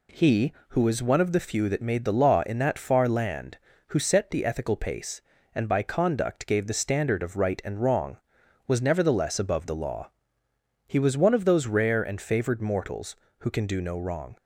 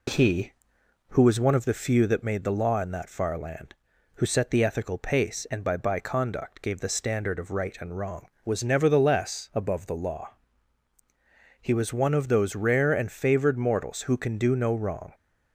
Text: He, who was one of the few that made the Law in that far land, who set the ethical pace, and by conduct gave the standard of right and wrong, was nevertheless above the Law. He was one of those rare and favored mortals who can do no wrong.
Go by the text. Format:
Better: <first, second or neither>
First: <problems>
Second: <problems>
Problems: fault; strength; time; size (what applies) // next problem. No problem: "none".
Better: first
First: none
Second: says "by" twice; at 5.7 s